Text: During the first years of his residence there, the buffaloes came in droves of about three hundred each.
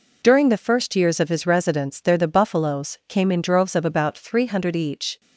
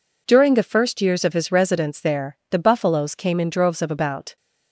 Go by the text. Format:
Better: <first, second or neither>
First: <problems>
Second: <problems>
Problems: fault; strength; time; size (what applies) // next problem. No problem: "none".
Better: first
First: none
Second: stops before "three hundred each"; at 4.3 s